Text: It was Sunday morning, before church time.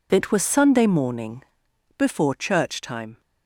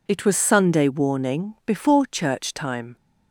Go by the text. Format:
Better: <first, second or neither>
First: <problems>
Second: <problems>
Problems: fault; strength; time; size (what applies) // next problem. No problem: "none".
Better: first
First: none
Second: says "warning" for "morning"; at 0.8 s